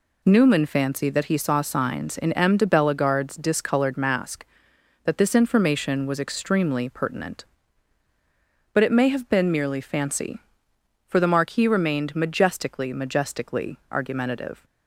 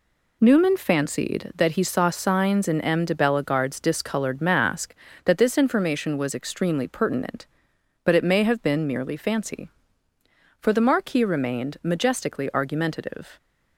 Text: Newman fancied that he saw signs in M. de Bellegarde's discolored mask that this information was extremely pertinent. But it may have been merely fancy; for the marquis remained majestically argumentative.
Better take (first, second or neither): second